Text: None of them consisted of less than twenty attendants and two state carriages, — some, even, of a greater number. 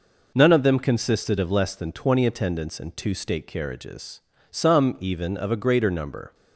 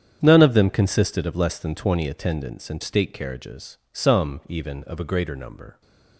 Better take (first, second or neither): first